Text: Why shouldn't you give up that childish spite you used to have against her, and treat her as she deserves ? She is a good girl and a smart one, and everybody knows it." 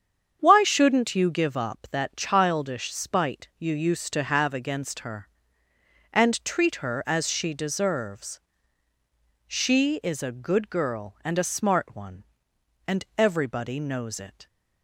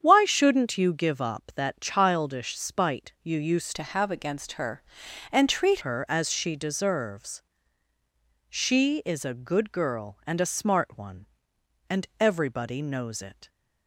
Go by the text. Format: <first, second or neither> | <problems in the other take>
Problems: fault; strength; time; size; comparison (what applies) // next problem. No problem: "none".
first | starts louder than the rest; strong; until 1.0 s; 8 dB; strong in the first // changes voice from "to" to "treat"; from 3.7 to 5.8 s; 2.1 s long